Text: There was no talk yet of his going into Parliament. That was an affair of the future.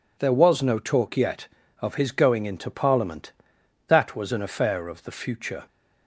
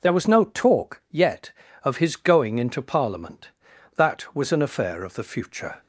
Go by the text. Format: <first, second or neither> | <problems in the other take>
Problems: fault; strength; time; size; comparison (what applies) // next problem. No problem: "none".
neither | none